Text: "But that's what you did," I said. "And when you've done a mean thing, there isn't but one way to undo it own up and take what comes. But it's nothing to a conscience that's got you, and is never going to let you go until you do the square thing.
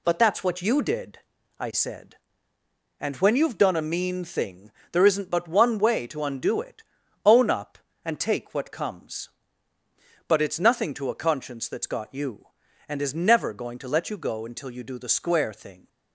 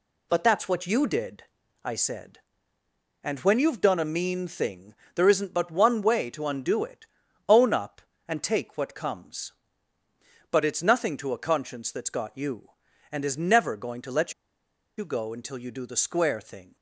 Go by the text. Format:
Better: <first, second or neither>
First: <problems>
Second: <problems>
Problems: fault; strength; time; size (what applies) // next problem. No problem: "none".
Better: first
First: pauses between "it" and "own"; at 6.8 s; 0.42 s long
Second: pauses between "it" and "own"; at 7.0 s; 0.42 s long // pauses between "let" and "you"; noticeable; at 14.3 s; 0.64 s long